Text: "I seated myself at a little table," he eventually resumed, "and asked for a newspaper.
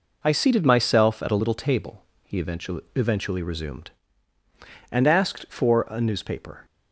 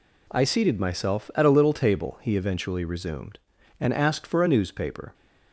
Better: second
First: says "eventually" twice; at 2.9 s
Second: none

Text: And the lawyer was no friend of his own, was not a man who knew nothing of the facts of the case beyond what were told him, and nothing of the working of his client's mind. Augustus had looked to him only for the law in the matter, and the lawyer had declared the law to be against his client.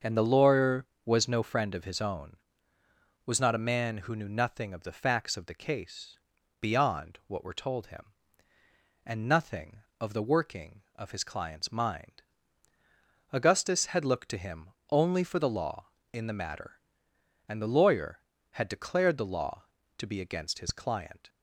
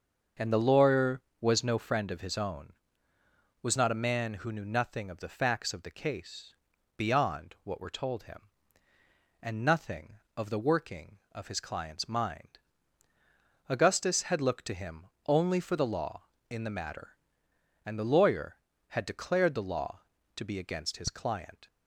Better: neither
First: starts louder than the rest; until 1.2 s; 6.5 dB // pauses between "case" and "beyond"; at 6.1 s; 0.42 s long // pauses between "him" and "only"; slight; at 14.6 s; 0.20 s long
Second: starts louder than the rest; until 1.5 s; 6.5 dB // pauses between "case" and "beyond"; at 6.5 s; 0.42 s long // pauses between "him" and "only"; slight; at 15.0 s; 0.20 s long

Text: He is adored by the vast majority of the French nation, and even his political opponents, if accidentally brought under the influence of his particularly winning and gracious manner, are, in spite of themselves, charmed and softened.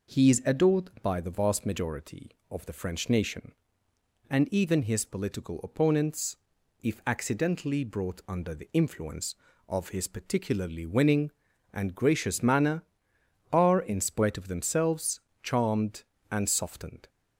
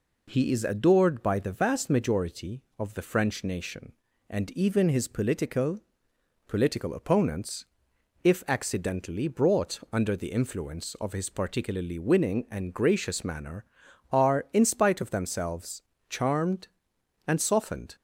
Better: first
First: none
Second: says "political" twice; at 6.4 s

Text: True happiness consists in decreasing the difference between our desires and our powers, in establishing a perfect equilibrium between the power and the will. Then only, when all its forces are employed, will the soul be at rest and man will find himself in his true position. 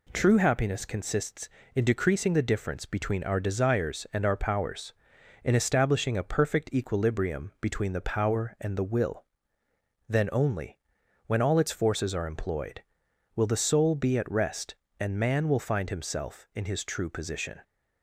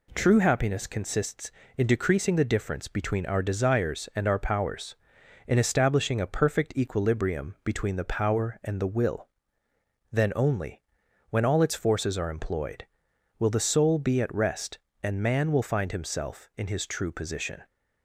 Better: neither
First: none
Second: none

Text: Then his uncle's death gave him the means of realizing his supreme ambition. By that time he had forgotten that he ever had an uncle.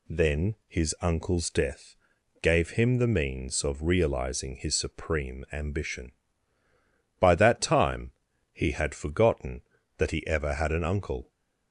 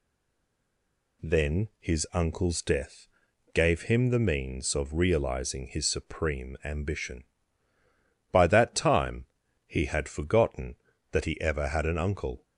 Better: first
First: pauses between "death" and "gave"; noticeable; at 1.9 s; 0.46 s long // pauses between "time" and "he"; at 8.1 s; 0.40 s long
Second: stays silent before the first word; noticeable; until 1.2 s; 1.2 s long // pauses between "death" and "gave"; noticeable; at 3.0 s; 0.46 s long // pauses between "time" and "he"; at 9.2 s; 0.40 s long

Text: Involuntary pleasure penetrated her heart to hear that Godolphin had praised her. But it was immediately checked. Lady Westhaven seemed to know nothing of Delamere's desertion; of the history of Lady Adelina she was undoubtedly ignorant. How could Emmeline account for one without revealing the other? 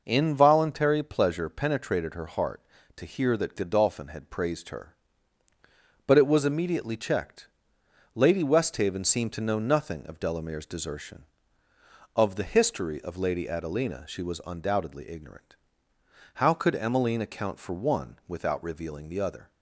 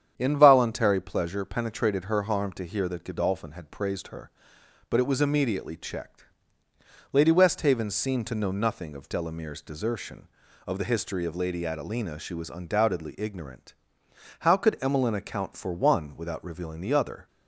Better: first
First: none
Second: starts louder than the rest; strong; until 1.1 s; 8.5 dB // says "harm" for "heart"; at 2.2 s

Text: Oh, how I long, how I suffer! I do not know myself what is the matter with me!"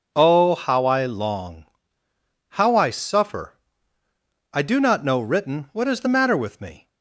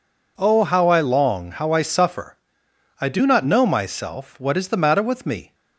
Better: second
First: says "written" for "myself"; at 5.1 s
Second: none

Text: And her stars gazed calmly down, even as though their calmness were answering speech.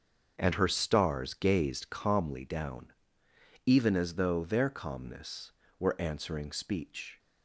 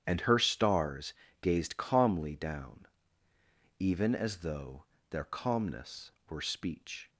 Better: first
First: starts louder than the rest; until 1.4 s; 6.5 dB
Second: starts louder than the rest; strong; until 1.0 s; 9.5 dB // pauses between "stars" and "gazed"; slight; at 1.1 s; 0.28 s long // pauses between "though" and "their"; slight; at 4.8 s; 0.24 s long // skips "answering"; at 6.4 s

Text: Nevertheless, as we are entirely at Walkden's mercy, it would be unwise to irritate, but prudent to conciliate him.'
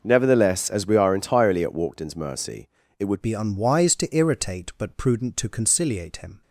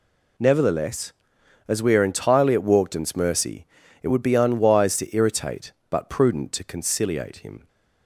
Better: second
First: changes voice at "be"; from 3.2 s on; 3.2 s long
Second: none

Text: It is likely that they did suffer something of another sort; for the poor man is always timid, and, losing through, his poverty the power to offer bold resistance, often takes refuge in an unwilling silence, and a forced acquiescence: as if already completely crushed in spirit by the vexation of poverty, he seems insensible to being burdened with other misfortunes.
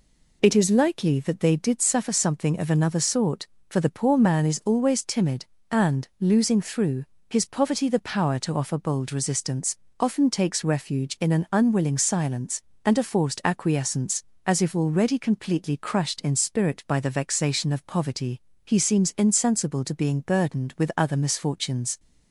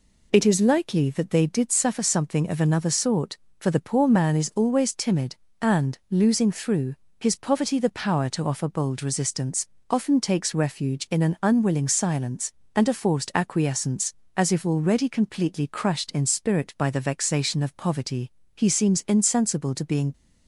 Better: first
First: none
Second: stops before "burdened with other misfortunes"; at 20.1 s

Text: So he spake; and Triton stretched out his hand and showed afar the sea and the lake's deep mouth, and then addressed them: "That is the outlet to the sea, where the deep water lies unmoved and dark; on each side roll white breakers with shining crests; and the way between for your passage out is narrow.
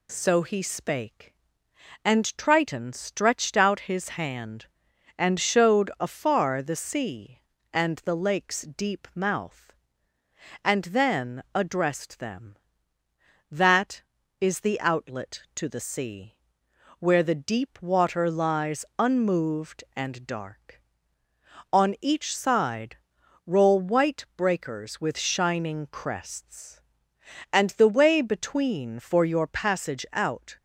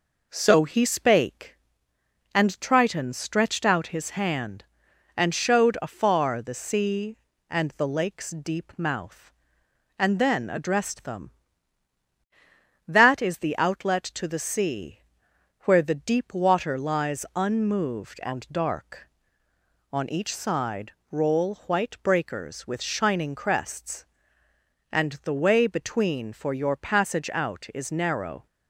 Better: second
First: pauses between "side" and "roll"; noticeable; at 22.9 s; 0.50 s long // stops before "is narrow"; at 30.5 s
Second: pauses between "side" and "roll"; slight; at 20.9 s; 0.18 s long

